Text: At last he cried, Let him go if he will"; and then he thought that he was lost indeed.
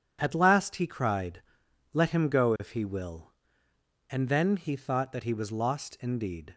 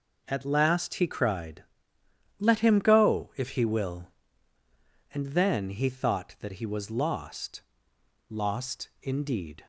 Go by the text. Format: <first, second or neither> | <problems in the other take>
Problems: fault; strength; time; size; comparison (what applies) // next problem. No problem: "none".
first | says "lost" twice; at 8.2 s